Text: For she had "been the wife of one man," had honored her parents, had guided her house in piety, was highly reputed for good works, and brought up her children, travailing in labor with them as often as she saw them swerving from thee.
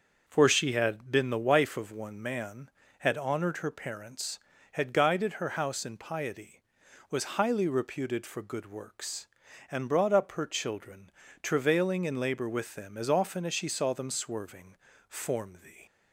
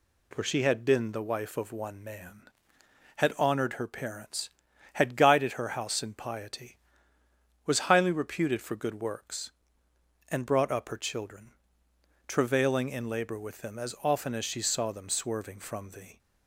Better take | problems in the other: second | starts louder than the rest; until 1.2 s; 6.5 dB // says "form" for "from"; at 15.0 s

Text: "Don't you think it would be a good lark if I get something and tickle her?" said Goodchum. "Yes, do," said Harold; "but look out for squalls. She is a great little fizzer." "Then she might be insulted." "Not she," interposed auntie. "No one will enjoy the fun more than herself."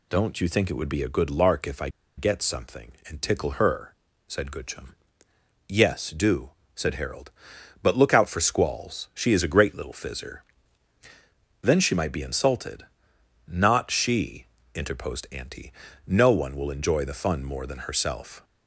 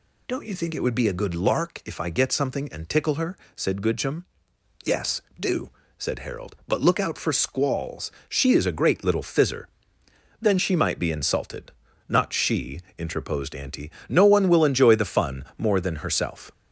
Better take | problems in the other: second | pauses between "I" and "get"; slight; at 1.8 s; 0.28 s long

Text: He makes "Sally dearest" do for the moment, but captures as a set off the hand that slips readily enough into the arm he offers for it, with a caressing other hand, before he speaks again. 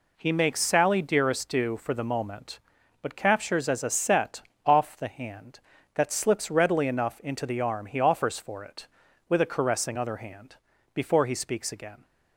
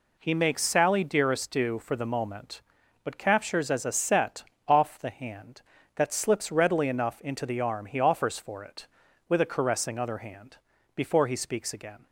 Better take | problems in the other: neither | pauses between "set" and "off"; slight; the same in both

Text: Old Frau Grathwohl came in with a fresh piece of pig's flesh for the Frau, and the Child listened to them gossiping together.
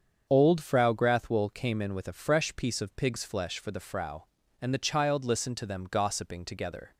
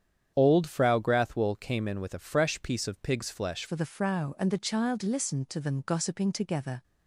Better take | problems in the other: first | starts louder than the rest; strong; until 1.3 s; 8.5 dB; strong in the first // changes voice at "for"; from 3.6 s on; 3.2 s long

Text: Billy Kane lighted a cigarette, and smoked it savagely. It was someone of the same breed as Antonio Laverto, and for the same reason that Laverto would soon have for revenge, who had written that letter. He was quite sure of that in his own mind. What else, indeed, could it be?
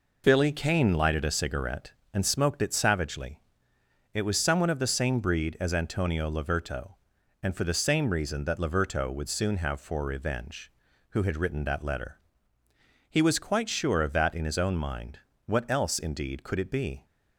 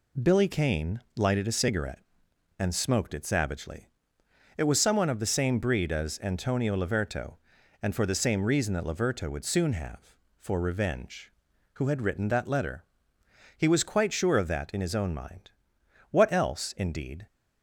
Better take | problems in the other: first | pauses between "Kane" and "lighted"; slight; at 1.0 s; 0.16 s long // stops before "could it be"; at 17.2 s

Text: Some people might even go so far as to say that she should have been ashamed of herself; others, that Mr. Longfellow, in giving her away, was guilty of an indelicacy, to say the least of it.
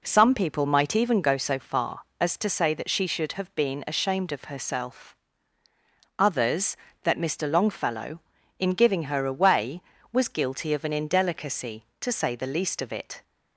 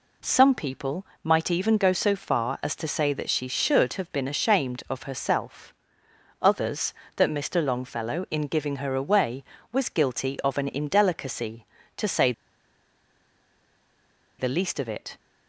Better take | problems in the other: first | pauses between "people" and "might"; slight; at 1.0 s; 0.20 s long // pauses between "say" and "the"; strong; at 12.3 s; 2.0 s long

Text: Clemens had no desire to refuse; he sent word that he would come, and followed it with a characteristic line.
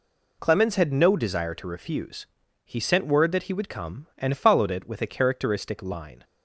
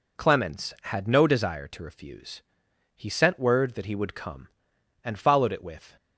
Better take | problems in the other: first | stops before "a characteristic line"; at 5.9 s

